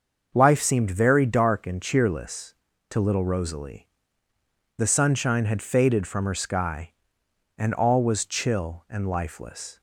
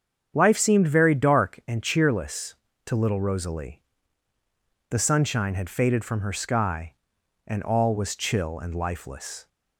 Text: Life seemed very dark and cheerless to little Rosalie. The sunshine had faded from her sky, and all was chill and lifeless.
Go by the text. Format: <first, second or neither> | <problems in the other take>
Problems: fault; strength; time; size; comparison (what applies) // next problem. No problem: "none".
neither | starts louder than the rest; the same in both